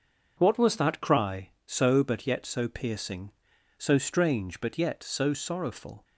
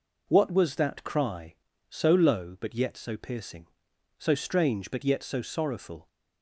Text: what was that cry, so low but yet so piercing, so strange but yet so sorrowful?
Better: second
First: starts louder than the rest; until 1.3 s; 7 dB // skips "low"; at 2.0 s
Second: none

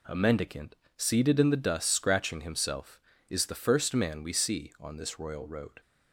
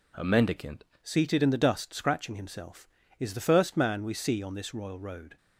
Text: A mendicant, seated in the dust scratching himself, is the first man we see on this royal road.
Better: first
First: none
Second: changes voice at "seated"; from 1.0 s on; 4.3 s long

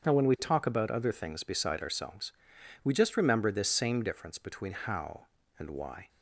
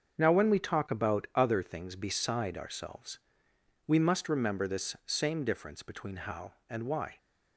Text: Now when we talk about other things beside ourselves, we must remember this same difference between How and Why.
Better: second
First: starts louder than the rest; until 1.0 s; 7 dB // says "just" for "must"; at 2.9 s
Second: starts louder than the rest; until 1.2 s; 6.5 dB

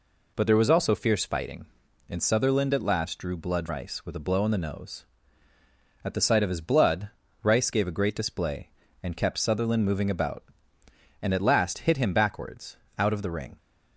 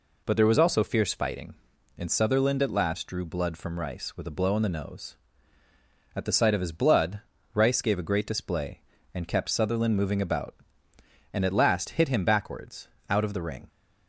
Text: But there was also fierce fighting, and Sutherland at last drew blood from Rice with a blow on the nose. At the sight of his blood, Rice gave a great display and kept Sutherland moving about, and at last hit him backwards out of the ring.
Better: second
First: skips "from"; at 3.6 s // pauses between "backwards" and "out"; slight; at 12.7 s; 0.22 s long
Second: pauses between "backwards" and "out"; slight; at 12.8 s; 0.22 s long

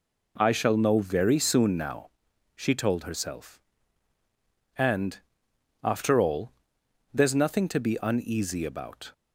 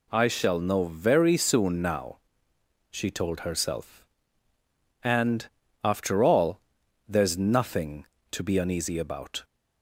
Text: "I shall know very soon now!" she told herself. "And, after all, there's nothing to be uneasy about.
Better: neither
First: none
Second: none

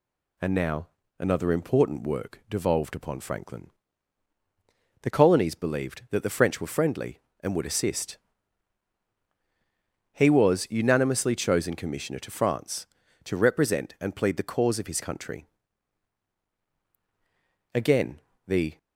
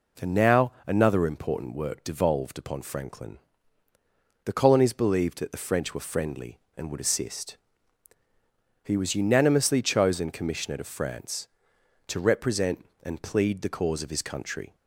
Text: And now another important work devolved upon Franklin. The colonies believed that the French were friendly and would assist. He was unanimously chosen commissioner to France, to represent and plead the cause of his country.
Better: second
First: pauses between "now" and "another"; slight; at 0.8 s; 0.32 s long // goes on to say "Again the"; noticeable; from 17.7 s on; 1.0 s long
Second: pauses between "now" and "another"; slight; at 0.7 s; 0.16 s long

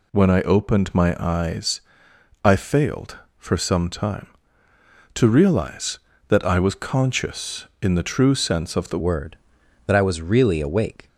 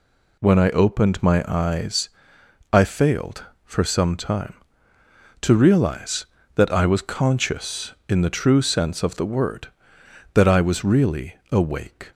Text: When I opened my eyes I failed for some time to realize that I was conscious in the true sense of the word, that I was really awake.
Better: second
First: pauses between "eyes" and "I"; noticeable; at 1.8 s; 0.62 s long // changes voice at "word"; from 8.9 s on; 2.1 s long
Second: pauses between "eyes" and "I"; noticeable; at 2.0 s; 0.62 s long

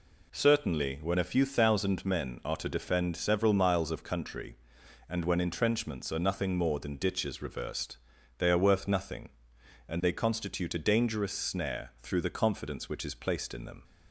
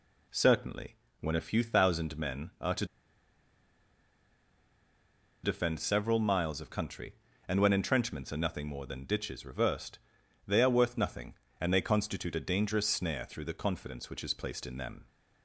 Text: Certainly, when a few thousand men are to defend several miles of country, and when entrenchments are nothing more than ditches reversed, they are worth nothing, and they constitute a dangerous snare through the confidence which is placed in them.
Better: first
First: none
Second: pauses between "to" and "defend"; strong; at 2.8 s; 2.5 s long

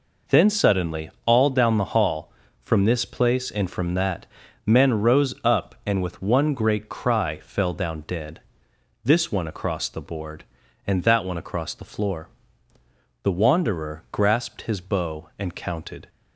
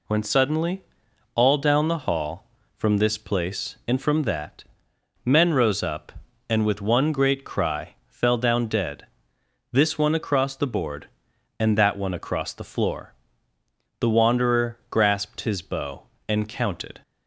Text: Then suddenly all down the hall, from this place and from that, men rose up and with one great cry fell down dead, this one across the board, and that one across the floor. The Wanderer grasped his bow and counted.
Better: first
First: none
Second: says "When" for "Then"; at 0.0 s // pauses between "suddenly" and "all"; noticeable; at 0.8 s; 0.52 s long

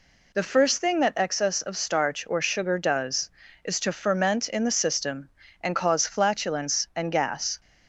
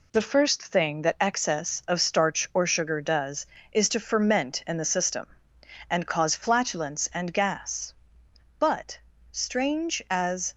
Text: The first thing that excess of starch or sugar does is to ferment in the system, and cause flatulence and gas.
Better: first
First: none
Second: goes on to say "But strange as"; strong; from 8.5 s on; 1.9 s long

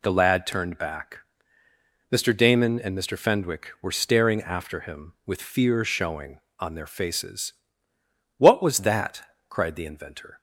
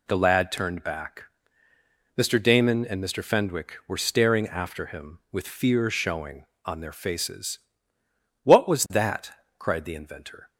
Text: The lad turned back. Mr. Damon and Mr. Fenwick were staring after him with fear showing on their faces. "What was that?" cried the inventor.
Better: neither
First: none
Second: none

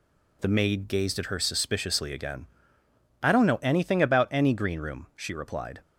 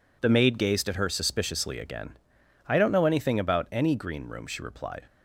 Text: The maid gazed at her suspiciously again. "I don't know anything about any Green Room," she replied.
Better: neither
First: none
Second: none

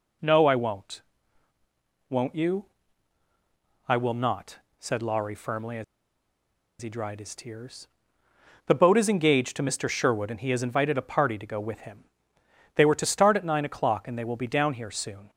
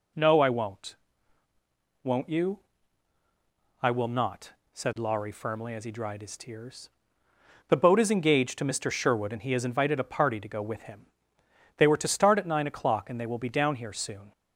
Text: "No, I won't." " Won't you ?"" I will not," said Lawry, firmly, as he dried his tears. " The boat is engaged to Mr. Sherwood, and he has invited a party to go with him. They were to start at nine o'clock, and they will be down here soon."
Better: second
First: pauses between "as" and "he"; noticeable; at 5.8 s; 0.97 s long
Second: none

